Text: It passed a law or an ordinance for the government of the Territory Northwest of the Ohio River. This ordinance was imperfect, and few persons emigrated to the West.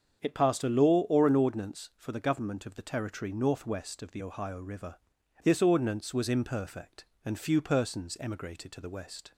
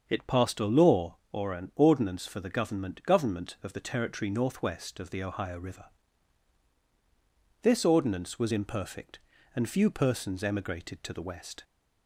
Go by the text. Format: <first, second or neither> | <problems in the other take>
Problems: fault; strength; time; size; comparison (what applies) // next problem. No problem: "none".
first | starts louder than the rest; until 1.0 s; 6.5 dB; strong in the first // says "government" twice; at 3.0 s